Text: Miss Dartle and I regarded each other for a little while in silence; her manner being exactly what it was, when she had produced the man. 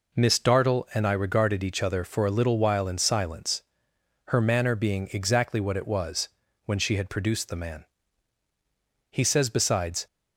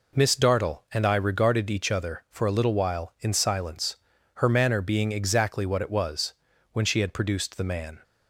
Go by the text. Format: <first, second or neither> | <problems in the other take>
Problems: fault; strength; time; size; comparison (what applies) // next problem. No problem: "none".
second | goes on to say "He says besides"; noticeable; from 9.0 s on; 0.98 s long